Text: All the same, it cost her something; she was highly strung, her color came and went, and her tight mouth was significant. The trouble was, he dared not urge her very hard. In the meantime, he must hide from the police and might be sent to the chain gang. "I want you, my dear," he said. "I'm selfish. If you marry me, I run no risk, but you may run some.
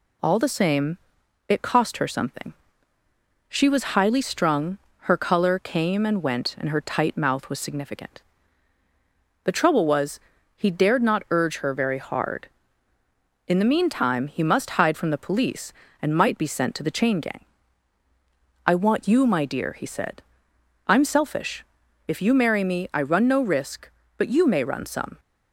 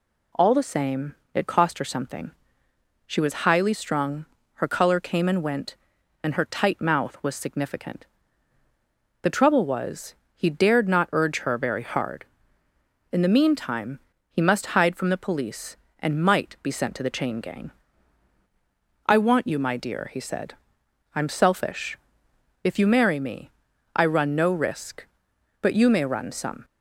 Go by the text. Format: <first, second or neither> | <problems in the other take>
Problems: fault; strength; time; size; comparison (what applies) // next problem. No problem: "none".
neither | none